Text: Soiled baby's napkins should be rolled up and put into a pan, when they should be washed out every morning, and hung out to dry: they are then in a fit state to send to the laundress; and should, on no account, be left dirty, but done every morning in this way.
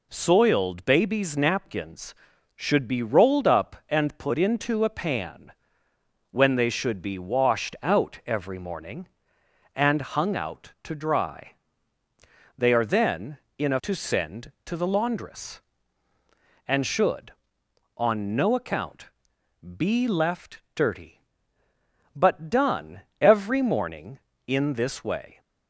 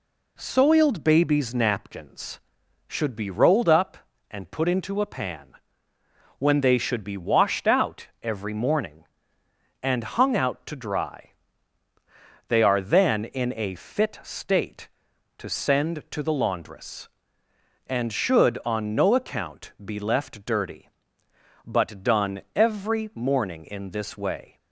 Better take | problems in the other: second | skips "fit state"; at 13.7 s // pauses between "done" and "every"; slight; at 22.9 s; 0.22 s long

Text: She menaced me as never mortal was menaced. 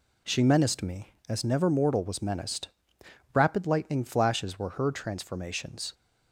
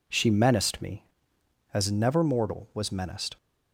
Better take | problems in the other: second | goes on to say "Rapid lightning flashes were her transformations"; strong; from 3.3 s on; 2.6 s long

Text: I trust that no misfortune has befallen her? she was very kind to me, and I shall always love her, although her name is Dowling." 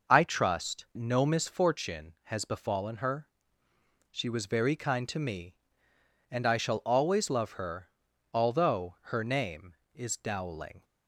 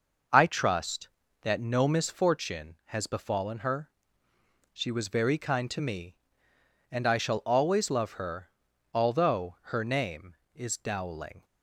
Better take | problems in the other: second | skips "that"; at 0.9 s // pauses between "although" and "her"; slight; at 8.9 s; 0.16 s long; slight in the second

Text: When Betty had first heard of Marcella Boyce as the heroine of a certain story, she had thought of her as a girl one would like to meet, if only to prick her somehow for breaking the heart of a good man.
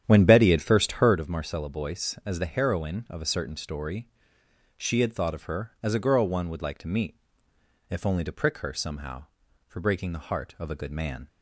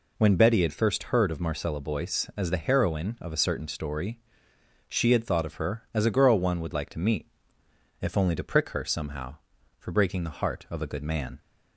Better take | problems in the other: second | starts louder than the rest; strong; until 1.2 s; 9.5 dB

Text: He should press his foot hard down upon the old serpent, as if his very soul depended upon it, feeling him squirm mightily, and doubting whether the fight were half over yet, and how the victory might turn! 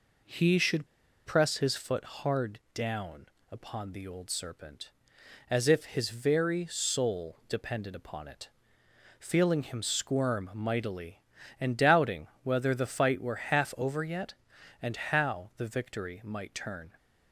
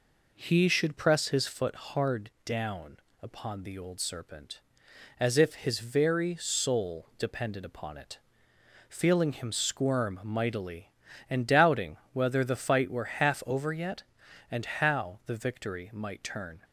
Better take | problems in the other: second | pauses between "should" and "press"; at 0.8 s; 0.39 s long // pauses between "down" and "upon"; slight; at 3.2 s; 0.24 s long; slight in the second // pauses between "doubting" and "whether"; slight; at 12.2 s; 0.16 s long; slight in the second

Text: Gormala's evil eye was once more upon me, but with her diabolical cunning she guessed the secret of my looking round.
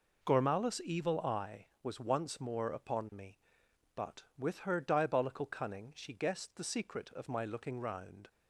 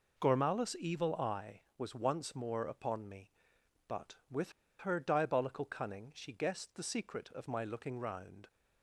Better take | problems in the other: first | pauses between "with" and "her"; slight; at 4.5 s; 0.26 s long

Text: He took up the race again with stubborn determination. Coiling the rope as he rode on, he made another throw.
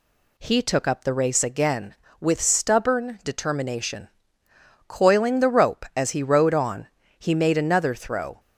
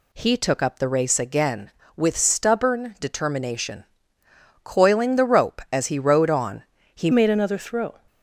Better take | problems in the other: first | changes voice at "made"; from 7.1 s on; 0.8 s long

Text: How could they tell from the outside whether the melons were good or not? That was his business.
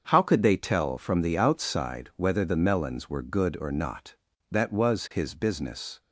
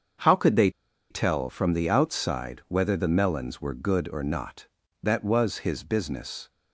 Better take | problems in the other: first | starts louder than the rest; until 1.6 s; 7 dB; also in the first // pauses between "they" and "tell"; at 0.6 s; 0.41 s long

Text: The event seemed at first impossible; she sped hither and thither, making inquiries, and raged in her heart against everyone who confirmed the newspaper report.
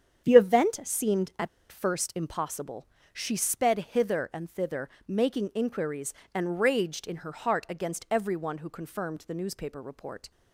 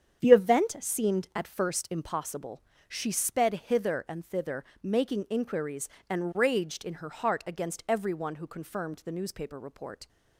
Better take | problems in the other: second | starts louder than the rest; strong; until 1.3 s; 8.5 dB; strong in the second // pauses between "at" and "first"; slight; at 1.4 s; 0.22 s long

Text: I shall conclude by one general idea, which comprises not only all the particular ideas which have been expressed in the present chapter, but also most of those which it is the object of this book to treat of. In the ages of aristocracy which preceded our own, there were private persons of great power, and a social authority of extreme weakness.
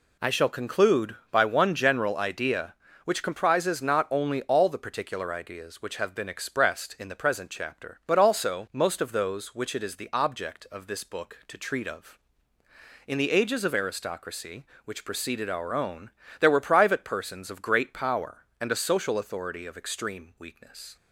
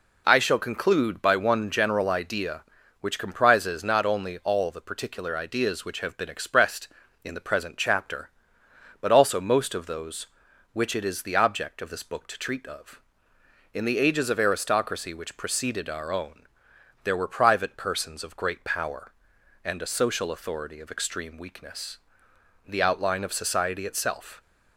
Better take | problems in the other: first | goes on to say "The outline of society itself"; strong; from 22.6 s on; 1.7 s long

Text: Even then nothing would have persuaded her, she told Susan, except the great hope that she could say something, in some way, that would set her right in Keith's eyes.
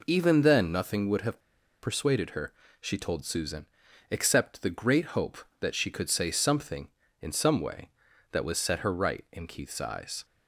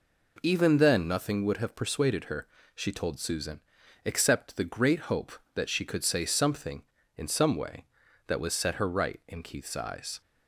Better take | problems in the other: second | pauses between "have" and "persuaded"; at 1.3 s; 0.43 s long

